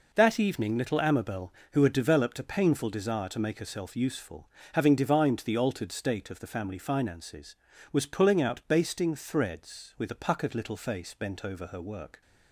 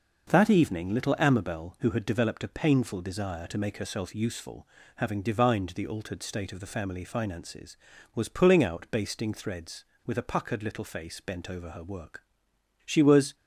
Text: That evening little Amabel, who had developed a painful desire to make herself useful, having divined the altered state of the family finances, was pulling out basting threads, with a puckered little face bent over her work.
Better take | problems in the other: first | starts louder than the rest; noticeable; until 1.3 s; 6 dB // goes on to say "She was"; slight; from 12.8 s on; 0.48 s long

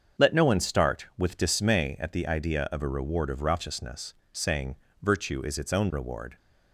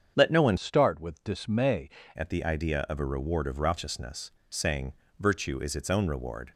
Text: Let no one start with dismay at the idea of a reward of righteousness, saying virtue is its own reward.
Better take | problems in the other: first | starts louder than the rest; strong; until 1.1 s; 7.5 dB; also in the first // changes voice from "start" to "dismay"; from 0.5 to 1.8 s; 1.3 s long // pauses between "saying" and "virtue"; slight; at 4.9 s; 0.26 s long; slight in the first

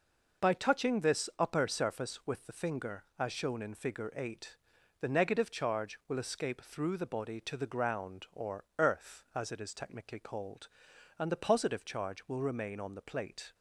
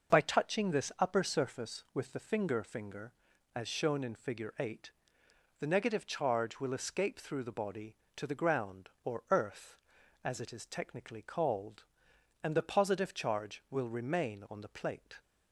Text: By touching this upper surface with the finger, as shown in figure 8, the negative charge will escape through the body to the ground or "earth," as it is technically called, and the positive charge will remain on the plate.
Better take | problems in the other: first | starts louder than the rest; noticeable; until 1.1 s; 6 dB // says "finger" twice; at 2.6 s

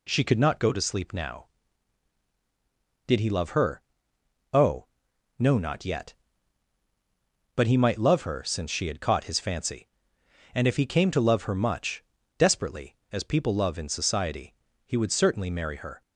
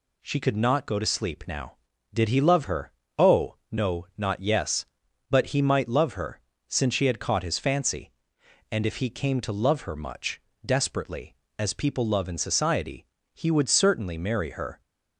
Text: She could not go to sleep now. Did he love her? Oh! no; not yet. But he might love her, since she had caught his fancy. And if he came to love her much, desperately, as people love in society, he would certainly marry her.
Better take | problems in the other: first | says "yes" for "yet"; at 4.4 s

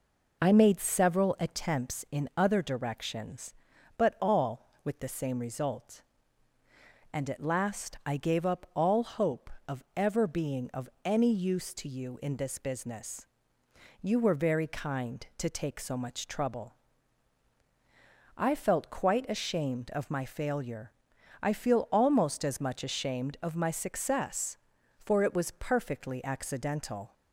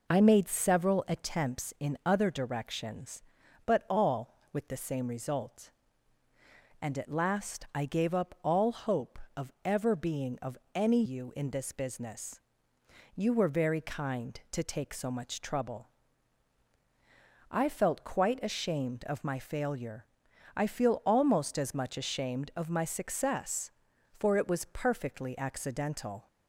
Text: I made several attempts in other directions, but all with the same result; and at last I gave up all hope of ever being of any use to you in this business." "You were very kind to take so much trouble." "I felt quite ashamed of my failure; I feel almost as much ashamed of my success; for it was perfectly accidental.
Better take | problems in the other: first | pauses between "of" and "any"; slight; at 10.5 s; 0.16 s long // skips "use to"; at 11.0 s

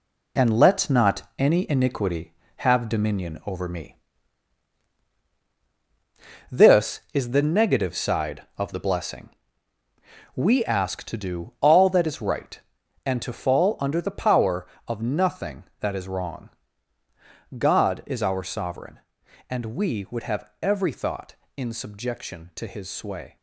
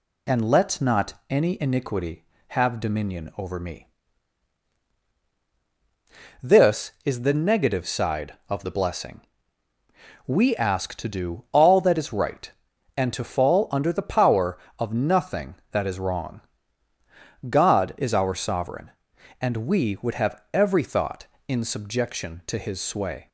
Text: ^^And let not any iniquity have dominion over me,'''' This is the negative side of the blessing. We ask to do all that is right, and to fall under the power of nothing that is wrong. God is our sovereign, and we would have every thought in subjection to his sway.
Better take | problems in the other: second | gets quieter; throughout; 6.5 dB // pauses between "not" and "any"; slight; at 1.2 s; 0.16 s long; slight in the second

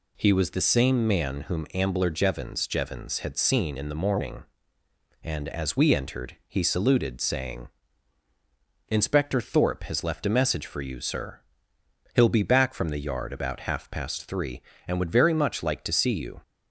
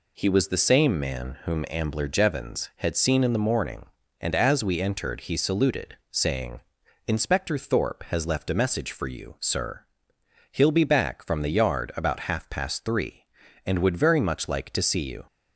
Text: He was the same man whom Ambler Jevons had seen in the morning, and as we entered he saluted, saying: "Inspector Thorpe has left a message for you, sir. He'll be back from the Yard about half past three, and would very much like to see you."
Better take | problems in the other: second | says "Jevons" twice; at 2.6 s

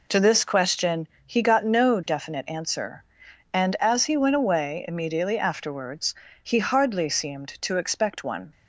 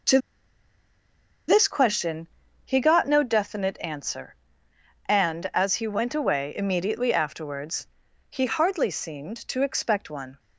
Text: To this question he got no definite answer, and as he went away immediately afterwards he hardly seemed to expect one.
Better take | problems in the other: first | pauses between "To" and "this"; strong; at 0.1 s; 1.3 s long // pauses between "question" and "he"; at 2.2 s; 0.38 s long; slight in the first // pauses between "afterwards" and "he"; noticeable; at 7.8 s; 0.46 s long; slight in the first

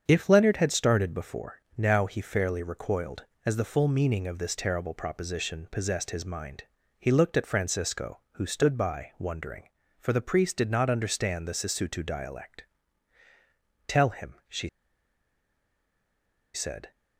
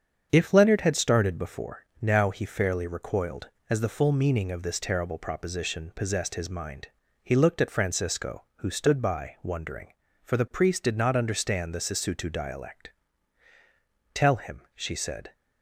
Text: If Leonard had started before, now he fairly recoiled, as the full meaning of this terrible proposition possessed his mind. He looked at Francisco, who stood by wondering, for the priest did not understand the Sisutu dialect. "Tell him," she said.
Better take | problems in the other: second | starts louder than the rest; strong; until 1.0 s; 7.5 dB; strong in the second // pauses between "she" and "said"; strong; at 14.6 s; 1.8 s long

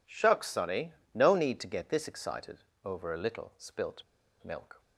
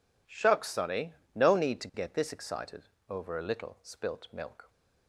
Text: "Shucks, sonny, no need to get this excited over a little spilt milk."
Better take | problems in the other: second | pauses between "excited" and "over"; slight; at 2.6 s; 0.24 s long; slight in the second // pauses between "spilt" and "milk"; at 4.0 s; 0.42 s long

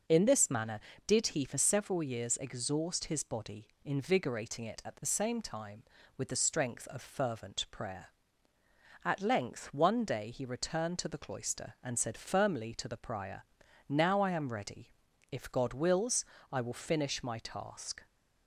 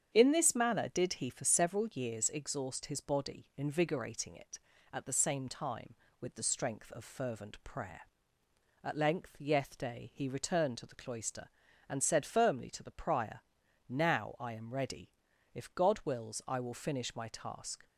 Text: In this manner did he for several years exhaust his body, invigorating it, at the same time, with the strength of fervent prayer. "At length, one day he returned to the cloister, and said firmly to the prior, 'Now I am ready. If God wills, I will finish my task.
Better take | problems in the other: first | starts louder than the rest; strong; until 1.1 s; 8 dB // says "yeth" for "one"; at 9.3 s

